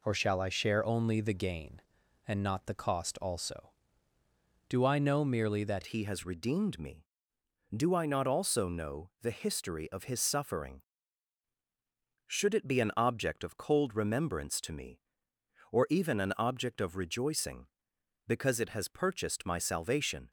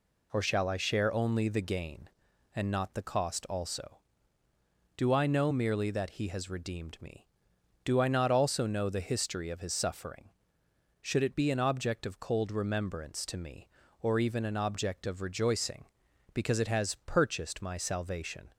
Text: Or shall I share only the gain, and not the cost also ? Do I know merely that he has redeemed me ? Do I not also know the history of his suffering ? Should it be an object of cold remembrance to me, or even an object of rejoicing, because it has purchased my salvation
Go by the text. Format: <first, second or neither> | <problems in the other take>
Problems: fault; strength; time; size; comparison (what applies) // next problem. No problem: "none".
second | changes voice at "he"; from 5.8 s on; 14.4 s long